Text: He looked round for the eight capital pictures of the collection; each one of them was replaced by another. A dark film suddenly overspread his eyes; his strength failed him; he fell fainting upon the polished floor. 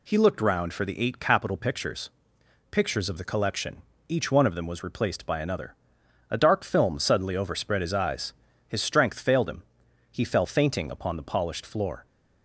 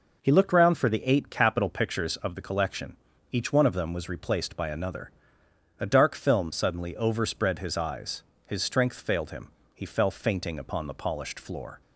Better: second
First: says "pictures" twice; at 2.7 s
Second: none

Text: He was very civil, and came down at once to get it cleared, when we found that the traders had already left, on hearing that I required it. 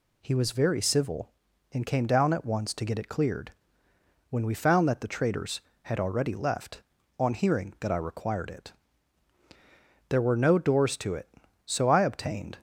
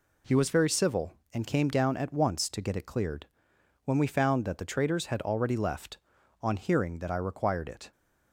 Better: second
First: goes on to say "There were no doors to it so I obtained"; strong; from 10.0 s on; 2.4 s long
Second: none

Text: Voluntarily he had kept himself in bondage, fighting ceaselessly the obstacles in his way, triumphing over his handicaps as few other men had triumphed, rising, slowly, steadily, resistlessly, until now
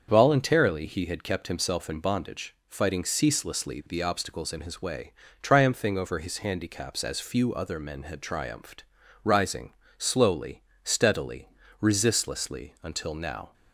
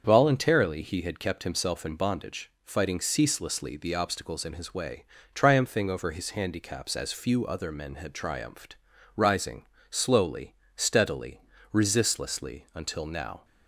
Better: neither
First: starts louder than the rest; until 1.1 s; 7 dB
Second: starts louder than the rest; until 1.0 s; 7 dB

